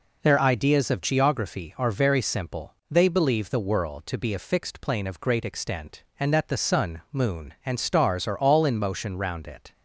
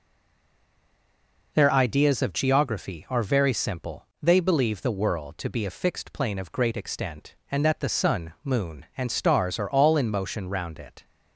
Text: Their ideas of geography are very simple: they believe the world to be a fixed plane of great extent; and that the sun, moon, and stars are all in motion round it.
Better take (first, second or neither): first